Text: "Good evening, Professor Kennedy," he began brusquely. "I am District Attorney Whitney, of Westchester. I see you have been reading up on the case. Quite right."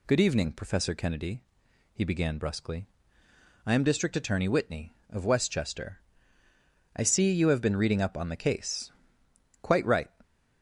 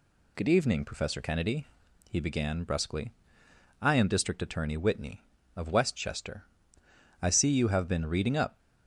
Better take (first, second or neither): first